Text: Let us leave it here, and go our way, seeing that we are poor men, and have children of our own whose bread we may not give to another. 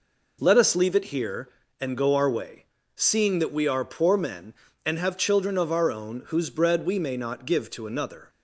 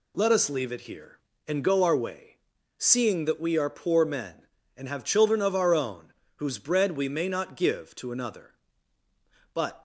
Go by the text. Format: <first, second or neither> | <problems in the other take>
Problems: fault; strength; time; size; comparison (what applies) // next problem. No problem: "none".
first | pauses between "own" and "whose"; slight; at 6.1 s; 0.22 s long // goes on to say "But"; slight; from 9.5 s on; 0.28 s long